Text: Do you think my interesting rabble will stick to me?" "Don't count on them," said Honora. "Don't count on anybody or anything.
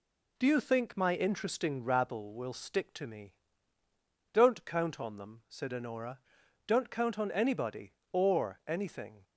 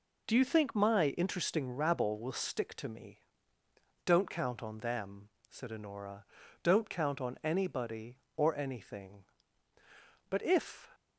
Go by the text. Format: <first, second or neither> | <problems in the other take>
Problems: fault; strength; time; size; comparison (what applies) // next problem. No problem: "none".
first | goes on to say "But if"; from 10.3 s on; 0.58 s long